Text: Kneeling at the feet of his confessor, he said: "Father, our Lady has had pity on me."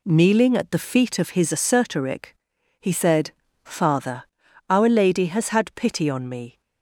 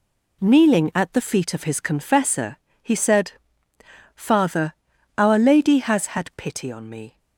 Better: second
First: says "assertoric" for "confessor"; at 1.5 s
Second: none

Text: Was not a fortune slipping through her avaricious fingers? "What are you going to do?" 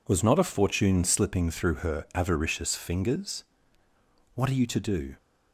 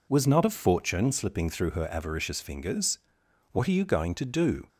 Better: second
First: skips "going"; at 4.6 s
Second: none

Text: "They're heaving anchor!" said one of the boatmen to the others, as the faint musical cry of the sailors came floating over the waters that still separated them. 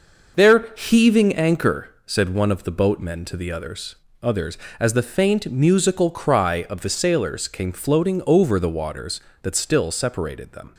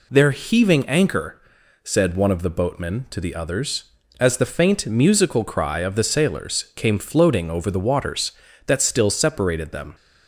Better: second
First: says "others" twice; at 4.2 s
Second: none

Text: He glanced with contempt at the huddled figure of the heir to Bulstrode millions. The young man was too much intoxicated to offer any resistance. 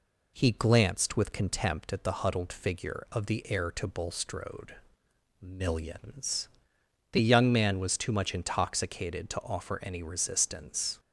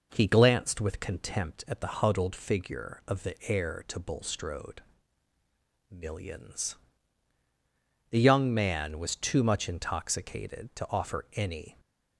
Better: first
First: pauses between "Bulstrode" and "millions"; noticeable; at 4.7 s; 0.66 s long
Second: pauses between "Bulstrode" and "millions"; at 4.8 s; 1.1 s long // stops before "resistance"; at 11.7 s

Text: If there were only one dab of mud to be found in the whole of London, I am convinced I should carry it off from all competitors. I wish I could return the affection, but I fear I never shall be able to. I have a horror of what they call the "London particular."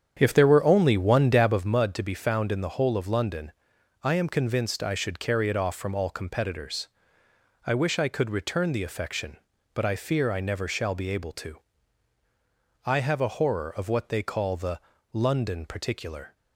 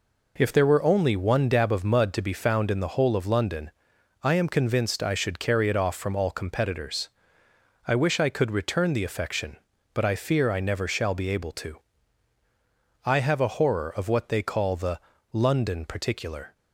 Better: second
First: starts louder than the rest; strong; until 1.7 s; 8.5 dB // pauses between "the" and "London"; slight; at 14.7 s; 0.32 s long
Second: pauses between "the" and "London"; slight; at 14.9 s; 0.32 s long

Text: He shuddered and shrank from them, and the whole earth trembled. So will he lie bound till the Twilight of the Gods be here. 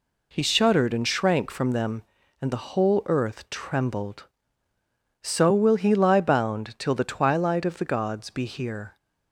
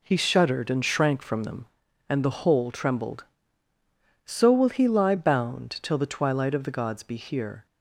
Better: first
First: none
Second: skips "earth"; at 2.7 s

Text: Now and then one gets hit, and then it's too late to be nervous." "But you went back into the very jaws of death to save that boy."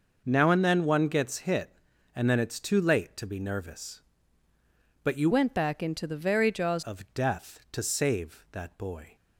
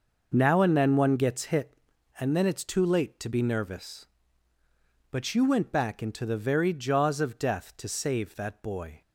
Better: second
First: changes voice from "went" to "jaws"; from 5.3 to 6.8 s; 1.5 s long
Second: none

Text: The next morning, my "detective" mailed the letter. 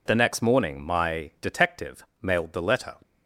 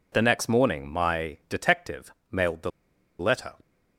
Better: first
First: none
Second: pauses between "detective" and "mailed"; slight; at 2.1 s; 0.16 s long // pauses between "the" and "letter"; noticeable; at 2.6 s; 0.49 s long

